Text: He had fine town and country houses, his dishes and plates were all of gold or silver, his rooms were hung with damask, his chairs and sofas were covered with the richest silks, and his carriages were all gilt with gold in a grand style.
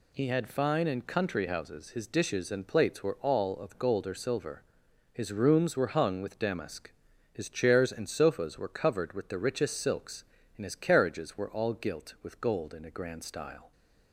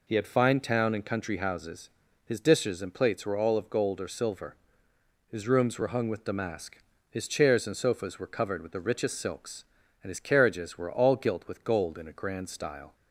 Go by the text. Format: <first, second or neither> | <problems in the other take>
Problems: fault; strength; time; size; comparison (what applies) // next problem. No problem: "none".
second | skips "town"; at 0.8 s